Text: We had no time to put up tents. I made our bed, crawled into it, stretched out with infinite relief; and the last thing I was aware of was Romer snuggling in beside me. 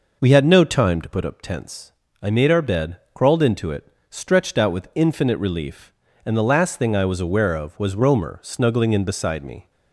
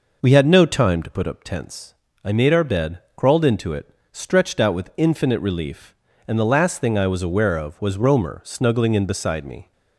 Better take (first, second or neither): neither